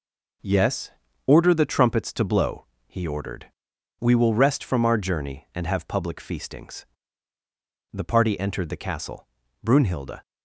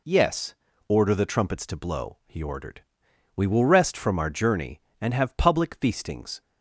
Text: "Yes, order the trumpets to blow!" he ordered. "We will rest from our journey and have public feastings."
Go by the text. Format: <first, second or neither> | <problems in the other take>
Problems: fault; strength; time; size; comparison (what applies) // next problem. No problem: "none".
second | goes on to say "The party entered the castle Brunhilde"; strong; from 7.9 s on; 2.3 s long